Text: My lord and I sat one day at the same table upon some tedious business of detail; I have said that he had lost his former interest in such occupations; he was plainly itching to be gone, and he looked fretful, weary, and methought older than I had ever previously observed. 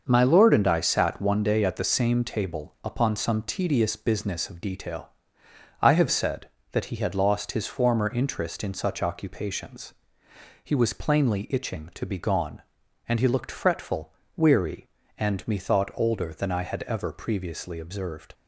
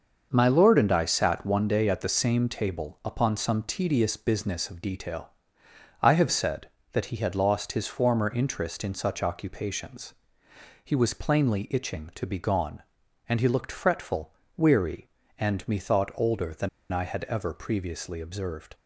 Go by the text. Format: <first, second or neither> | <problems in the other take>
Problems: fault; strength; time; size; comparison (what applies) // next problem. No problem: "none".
first | starts louder than the rest; until 1.3 s; 6 dB; also in the first // pauses between "than" and "I"; slight; at 16.6 s; 0.23 s long